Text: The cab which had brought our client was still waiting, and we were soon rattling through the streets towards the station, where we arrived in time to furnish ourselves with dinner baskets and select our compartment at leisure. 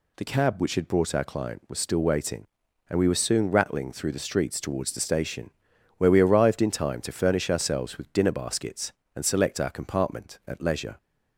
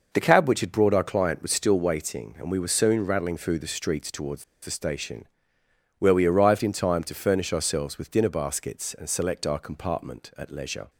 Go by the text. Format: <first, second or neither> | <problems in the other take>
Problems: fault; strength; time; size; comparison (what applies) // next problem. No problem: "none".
first | pauses between "towards" and "the"; slight; at 4.4 s; 0.19 s long